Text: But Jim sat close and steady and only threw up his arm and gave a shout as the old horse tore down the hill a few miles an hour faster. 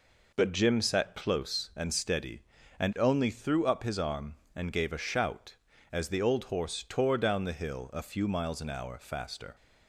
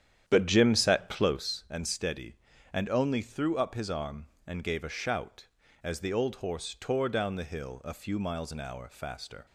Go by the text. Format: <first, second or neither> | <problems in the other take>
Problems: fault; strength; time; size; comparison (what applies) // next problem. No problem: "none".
first | starts louder than the rest; strong; until 1.6 s; 9.5 dB